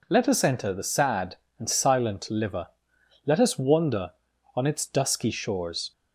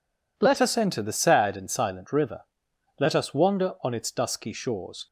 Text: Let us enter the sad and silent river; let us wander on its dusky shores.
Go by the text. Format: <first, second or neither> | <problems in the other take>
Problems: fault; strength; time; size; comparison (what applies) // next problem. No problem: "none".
second | says "liver" for "river"; at 2.2 s